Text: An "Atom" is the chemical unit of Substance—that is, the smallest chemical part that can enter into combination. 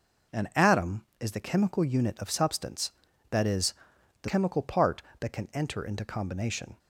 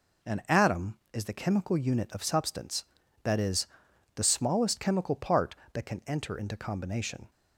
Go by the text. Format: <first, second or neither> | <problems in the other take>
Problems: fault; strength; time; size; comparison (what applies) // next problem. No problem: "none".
second | skips "smallest"; at 4.2 s